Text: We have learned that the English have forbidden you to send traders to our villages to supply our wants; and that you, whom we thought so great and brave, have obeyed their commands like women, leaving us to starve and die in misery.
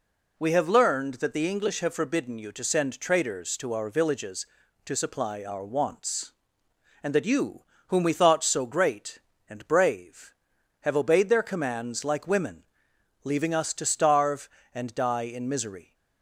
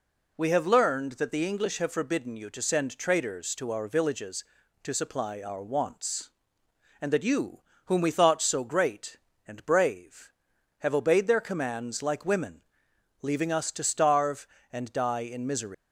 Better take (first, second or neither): first